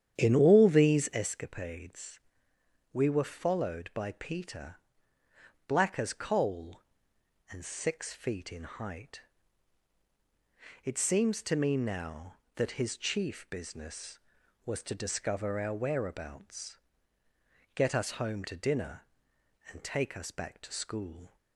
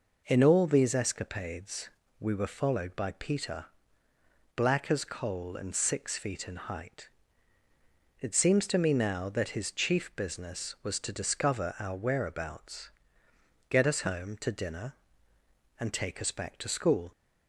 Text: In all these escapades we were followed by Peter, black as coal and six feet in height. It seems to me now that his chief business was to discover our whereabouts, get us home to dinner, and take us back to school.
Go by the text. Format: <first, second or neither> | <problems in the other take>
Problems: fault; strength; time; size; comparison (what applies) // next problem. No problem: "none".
second | starts louder than the rest; strong; until 1.3 s; 9.5 dB // pauses between "escapades" and "we"; noticeable; at 2.1 s; 0.74 s long; slight in the second